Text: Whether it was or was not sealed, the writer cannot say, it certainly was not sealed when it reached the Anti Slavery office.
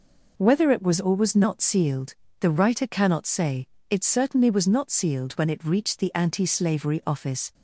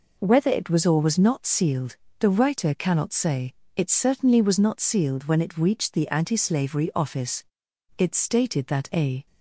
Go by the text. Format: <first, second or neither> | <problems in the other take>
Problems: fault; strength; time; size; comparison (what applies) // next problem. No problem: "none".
first | goes on to say "It stated that a"; noticeable; from 7.9 s on; 1.2 s long